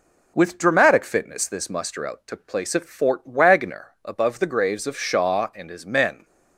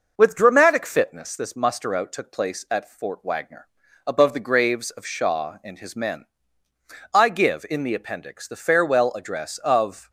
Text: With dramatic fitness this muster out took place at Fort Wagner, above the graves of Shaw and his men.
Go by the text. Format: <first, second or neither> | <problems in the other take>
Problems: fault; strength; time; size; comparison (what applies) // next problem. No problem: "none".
first | goes on to say "I give in the Appendix the farewell address of"; strong; from 7.1 s on; 2.9 s long